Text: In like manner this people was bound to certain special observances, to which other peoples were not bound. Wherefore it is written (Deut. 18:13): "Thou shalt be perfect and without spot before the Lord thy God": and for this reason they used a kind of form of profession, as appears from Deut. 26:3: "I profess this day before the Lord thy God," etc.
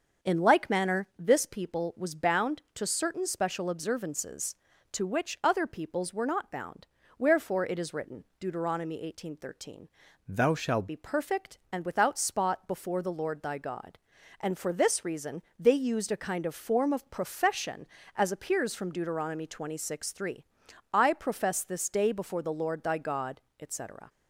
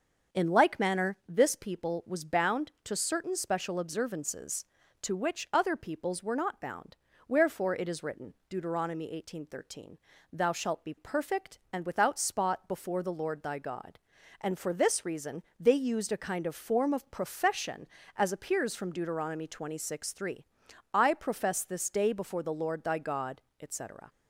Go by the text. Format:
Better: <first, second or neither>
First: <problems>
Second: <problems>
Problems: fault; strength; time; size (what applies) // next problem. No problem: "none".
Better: second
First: starts louder than the rest; until 1.3 s; 6.5 dB // changes voice from "Thou" to "shalt"; from 10.2 to 10.8 s; 0.6 s long // pauses between "reason" and "they"; slight; at 15.4 s; 0.16 s long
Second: starts louder than the rest; until 1.4 s; 7 dB // pauses between "reason" and "they"; slight; at 15.4 s; 0.16 s long